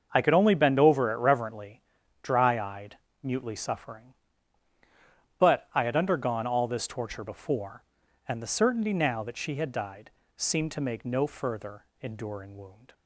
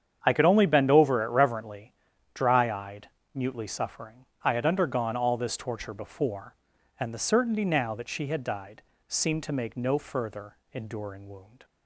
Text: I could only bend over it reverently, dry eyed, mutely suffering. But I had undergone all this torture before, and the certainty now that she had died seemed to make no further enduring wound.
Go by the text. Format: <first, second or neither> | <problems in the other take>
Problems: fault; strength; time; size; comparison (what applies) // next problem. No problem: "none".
first | starts louder than the rest; strong; until 1.2 s; 8.5 dB; also in the first // skips "But"; at 4.3 s // pauses between "died" and "seemed"; slight; at 8.8 s; 0.26 s long; slight in the first // pauses between "further" and "enduring"; slight; at 10.5 s; 0.18 s long; slight in the first